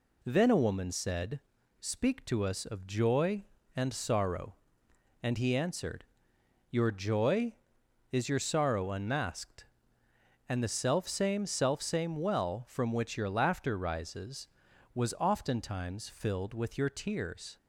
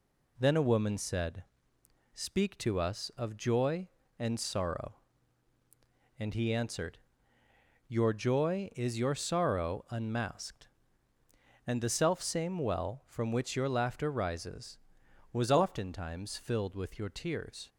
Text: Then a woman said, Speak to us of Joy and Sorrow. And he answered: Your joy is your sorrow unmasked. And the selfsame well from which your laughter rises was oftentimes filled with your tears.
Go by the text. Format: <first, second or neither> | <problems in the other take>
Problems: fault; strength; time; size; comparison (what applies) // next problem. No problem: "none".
second | says "selfsame" twice; at 11.4 s